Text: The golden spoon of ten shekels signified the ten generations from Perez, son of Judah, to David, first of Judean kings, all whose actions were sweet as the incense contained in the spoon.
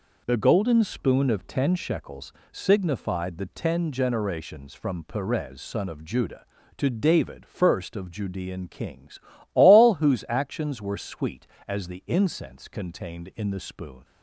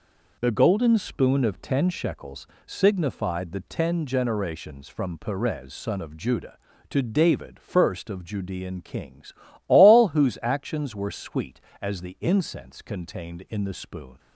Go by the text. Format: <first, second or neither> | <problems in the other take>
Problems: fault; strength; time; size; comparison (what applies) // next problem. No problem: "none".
neither | pauses between "shekels" and "signified"; slight; the same in both